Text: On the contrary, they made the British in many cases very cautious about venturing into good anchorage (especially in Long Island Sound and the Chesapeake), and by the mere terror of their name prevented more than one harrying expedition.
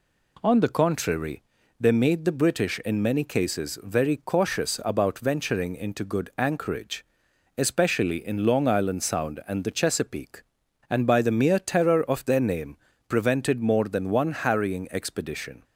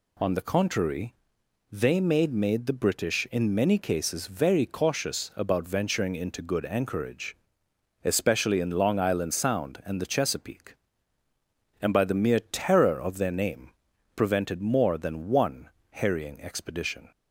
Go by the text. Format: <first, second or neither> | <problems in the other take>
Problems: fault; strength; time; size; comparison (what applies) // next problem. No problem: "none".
first | says "made" twice; at 2.3 s // pauses between "name" and "prevented"; noticeable; at 13.6 s; 0.46 s long; slight in the first // pauses between "one" and "harrying"; slight; at 15.6 s; 0.20 s long